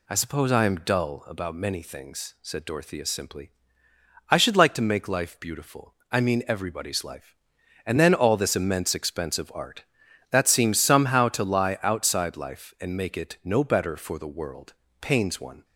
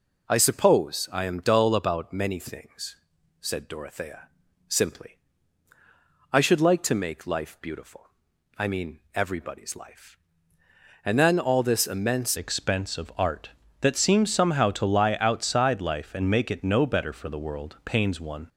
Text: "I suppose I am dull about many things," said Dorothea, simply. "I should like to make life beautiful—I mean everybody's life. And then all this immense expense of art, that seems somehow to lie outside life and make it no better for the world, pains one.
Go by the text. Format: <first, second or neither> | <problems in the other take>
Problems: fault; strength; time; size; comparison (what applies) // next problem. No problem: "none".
first | changes voice at "expense"; from 12.3 s on; 6.1 s long